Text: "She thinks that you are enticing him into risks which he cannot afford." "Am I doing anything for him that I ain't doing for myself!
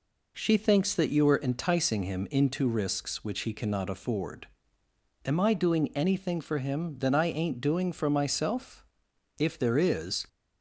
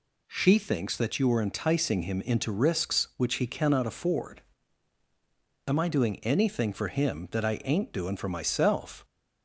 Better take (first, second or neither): second